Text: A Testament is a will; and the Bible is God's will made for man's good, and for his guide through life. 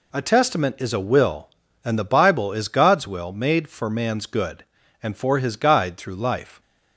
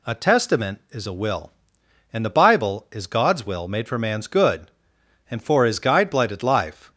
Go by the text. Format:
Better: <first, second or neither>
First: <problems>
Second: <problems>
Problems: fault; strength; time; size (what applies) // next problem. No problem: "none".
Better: first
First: none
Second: says "blighted" for "through"; at 6.1 s